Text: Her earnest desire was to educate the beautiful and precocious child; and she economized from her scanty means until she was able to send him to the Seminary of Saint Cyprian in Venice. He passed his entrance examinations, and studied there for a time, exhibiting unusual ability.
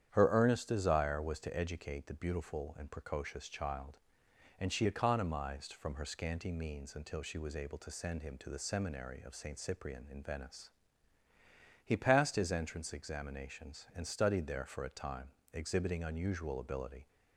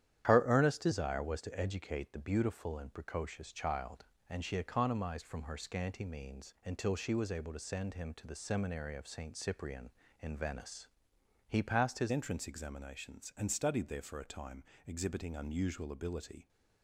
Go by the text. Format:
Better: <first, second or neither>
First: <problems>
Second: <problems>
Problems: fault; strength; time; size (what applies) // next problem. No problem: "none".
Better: first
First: starts louder than the rest; strong; until 1.1 s; 9 dB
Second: starts louder than the rest; strong; until 1.3 s; 10.5 dB // changes voice at "entrance"; from 12.1 s on; 4.3 s long